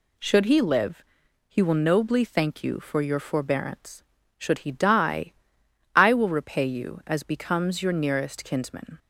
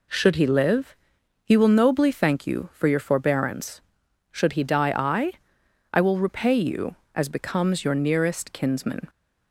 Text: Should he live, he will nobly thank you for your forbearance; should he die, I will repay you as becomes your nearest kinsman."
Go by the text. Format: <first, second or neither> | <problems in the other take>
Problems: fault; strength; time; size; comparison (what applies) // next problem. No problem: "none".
first | says "I" twice; at 5.9 s